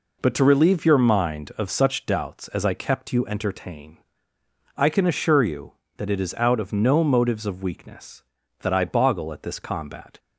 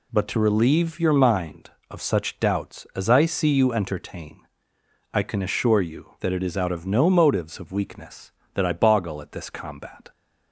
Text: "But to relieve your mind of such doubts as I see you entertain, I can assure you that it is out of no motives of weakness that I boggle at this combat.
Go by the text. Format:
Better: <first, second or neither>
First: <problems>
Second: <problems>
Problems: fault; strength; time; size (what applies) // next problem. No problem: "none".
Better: second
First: says "kept" for "see"; at 2.7 s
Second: none